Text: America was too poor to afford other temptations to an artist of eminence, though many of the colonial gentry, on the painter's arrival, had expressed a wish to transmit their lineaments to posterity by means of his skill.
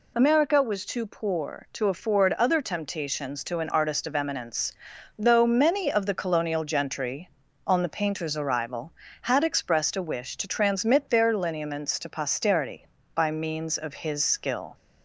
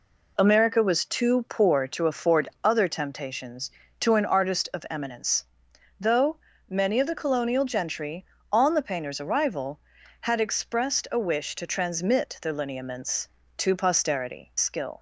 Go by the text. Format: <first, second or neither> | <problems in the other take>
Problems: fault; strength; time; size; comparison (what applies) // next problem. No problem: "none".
first | pauses between "though" and "many"; slight; at 6.3 s; 0.32 s long // skips "by means of his"; at 14.5 s